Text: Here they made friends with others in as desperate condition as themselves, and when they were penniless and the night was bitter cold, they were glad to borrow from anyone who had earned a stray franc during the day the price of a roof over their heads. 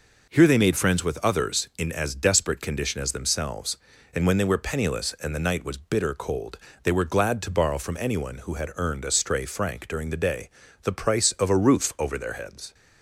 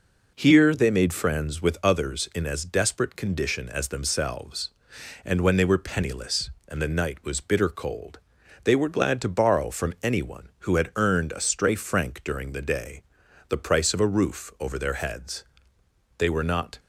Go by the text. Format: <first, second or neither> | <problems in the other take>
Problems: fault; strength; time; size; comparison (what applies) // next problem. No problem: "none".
first | pauses between "day" and "the"; noticeable; at 13.0 s; 0.46 s long; slight in the first // goes on to say "They were not"; noticeable; from 16.1 s on; 0.62 s long